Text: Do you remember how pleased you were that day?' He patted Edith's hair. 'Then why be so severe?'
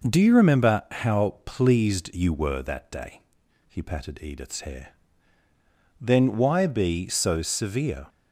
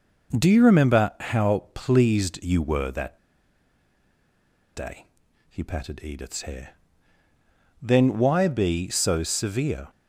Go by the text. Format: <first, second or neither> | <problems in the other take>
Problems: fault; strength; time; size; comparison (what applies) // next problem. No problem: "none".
first | pauses between "that" and "day"; strong; at 3.1 s; 1.5 s long